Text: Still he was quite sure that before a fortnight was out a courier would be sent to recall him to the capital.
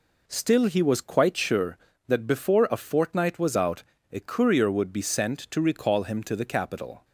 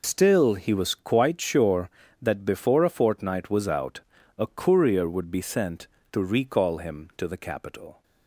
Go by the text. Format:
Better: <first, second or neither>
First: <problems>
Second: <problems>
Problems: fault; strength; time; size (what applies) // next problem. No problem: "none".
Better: first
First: pauses between "out" and "a"; slight; at 3.8 s; 0.28 s long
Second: loses the start of "Still"; at 0.0 s; 105 ms // pauses between "out" and "a"; slight; at 3.9 s; 0.36 s long